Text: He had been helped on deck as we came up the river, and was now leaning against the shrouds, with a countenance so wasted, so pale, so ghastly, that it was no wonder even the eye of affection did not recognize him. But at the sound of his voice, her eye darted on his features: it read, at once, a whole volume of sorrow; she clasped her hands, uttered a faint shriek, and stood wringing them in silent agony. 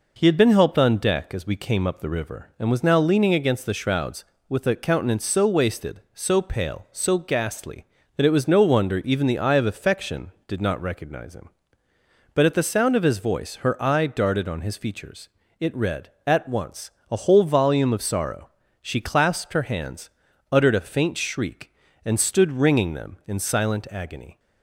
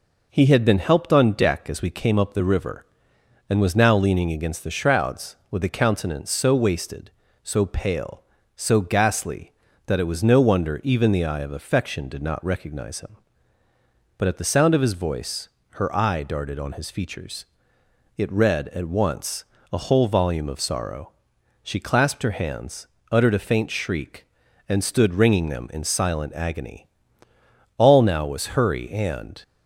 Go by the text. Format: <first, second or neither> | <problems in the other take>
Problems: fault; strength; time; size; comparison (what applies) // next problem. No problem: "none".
first | goes on to say "All now was hurry and"; from 27.7 s on; 1.6 s long